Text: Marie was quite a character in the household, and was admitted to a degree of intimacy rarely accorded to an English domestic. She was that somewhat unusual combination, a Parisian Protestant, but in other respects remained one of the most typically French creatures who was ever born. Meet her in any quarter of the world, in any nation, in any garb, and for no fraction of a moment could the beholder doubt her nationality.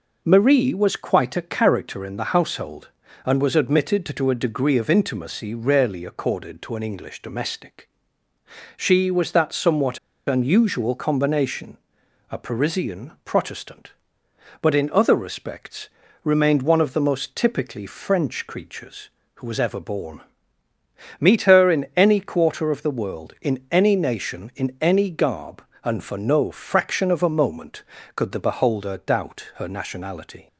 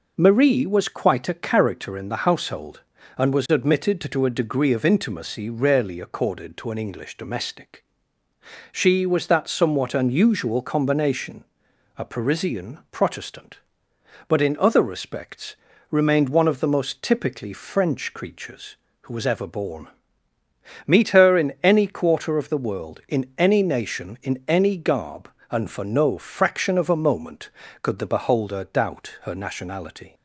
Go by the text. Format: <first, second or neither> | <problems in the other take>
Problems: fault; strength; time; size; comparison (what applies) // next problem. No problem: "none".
second | pauses between "somewhat" and "unusual"; slight; at 9.9 s; 0.28 s long // pauses between "respects" and "remained"; slight; at 15.8 s; 0.34 s long; slight in the second